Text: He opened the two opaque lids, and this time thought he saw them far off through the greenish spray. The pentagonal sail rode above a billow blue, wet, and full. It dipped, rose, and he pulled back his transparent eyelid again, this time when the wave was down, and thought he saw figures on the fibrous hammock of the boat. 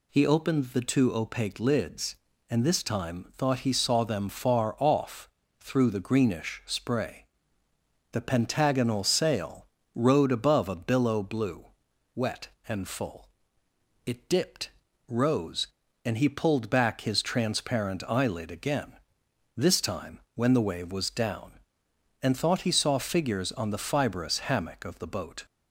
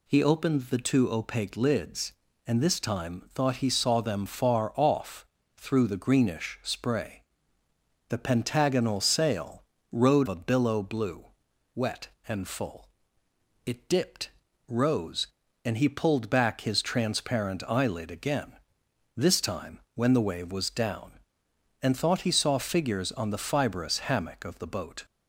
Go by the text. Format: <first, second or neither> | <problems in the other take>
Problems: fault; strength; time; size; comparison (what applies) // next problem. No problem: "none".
first | pauses between "off" and "through"; slight; at 5.2 s; 0.32 s long; slight in the first // pauses between "sail" and "rode"; slight; at 9.6 s; 0.28 s long; slight in the first // skips "above"; at 10.2 s